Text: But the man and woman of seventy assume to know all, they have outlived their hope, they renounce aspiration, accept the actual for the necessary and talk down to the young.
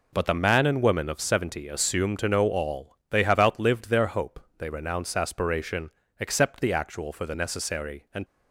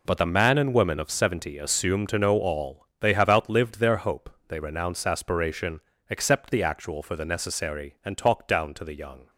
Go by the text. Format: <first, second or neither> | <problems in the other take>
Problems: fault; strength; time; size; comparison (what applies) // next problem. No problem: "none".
second | stops before "talk down to the young"; at 8.2 s